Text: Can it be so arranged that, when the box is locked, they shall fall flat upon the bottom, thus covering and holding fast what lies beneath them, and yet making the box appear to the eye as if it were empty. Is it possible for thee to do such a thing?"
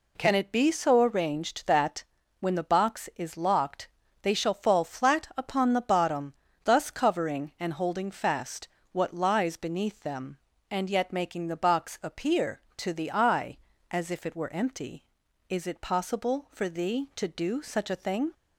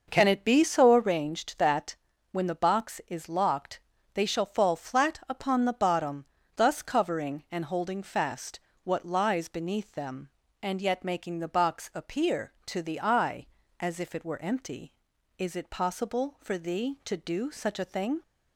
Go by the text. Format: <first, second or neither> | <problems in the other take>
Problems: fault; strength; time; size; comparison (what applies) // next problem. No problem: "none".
first | starts louder than the rest; noticeable; until 1.3 s; 6 dB // pauses between "fast" and "what"; slight; at 8.5 s; 0.26 s long; slight in the first